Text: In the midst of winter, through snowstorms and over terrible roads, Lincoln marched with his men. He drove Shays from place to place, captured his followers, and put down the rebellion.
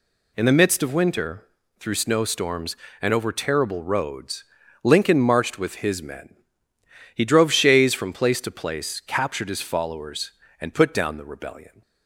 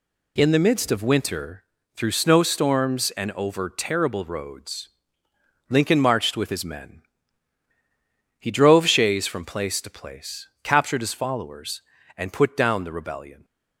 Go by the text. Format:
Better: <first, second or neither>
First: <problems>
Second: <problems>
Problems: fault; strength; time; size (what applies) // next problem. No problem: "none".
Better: neither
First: none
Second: none